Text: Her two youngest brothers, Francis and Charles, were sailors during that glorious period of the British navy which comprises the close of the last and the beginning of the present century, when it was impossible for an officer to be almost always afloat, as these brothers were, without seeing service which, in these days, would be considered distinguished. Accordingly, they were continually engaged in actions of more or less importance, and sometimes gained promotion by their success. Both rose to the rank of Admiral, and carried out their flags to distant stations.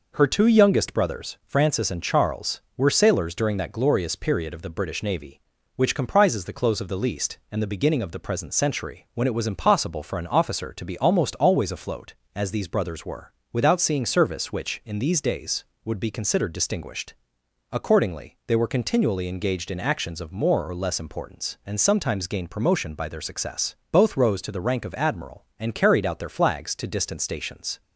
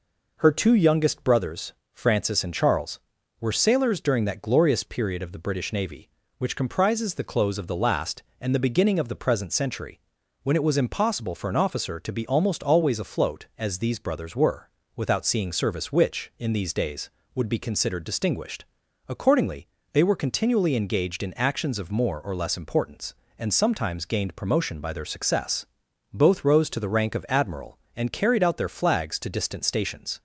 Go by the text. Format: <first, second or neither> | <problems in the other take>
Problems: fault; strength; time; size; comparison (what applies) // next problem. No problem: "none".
second | says "least" for "last"; at 6.9 s